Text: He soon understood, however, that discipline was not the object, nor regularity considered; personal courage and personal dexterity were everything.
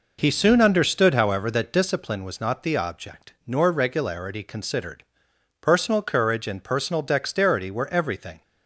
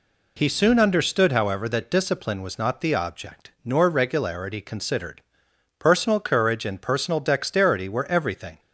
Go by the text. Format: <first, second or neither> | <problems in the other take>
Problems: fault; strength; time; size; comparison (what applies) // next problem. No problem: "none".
second | starts louder than the rest; noticeable; until 2.0 s; 5 dB